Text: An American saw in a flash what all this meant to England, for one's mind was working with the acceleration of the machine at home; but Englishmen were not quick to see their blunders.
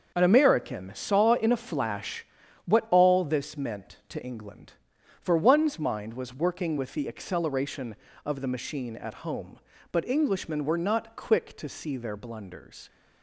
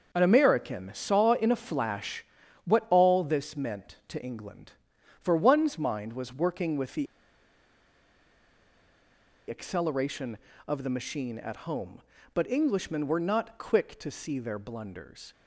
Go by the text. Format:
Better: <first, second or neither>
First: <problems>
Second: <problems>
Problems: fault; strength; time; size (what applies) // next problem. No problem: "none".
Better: first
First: starts louder than the rest; until 1.1 s; 6.5 dB // pauses between "flash" and "what"; at 2.2 s; 0.38 s long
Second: starts louder than the rest; until 1.1 s; 6.5 dB // pauses between "flash" and "what"; at 2.2 s; 0.38 s long // pauses between "the" and "acceleration"; strong; at 7.0 s; 2.4 s long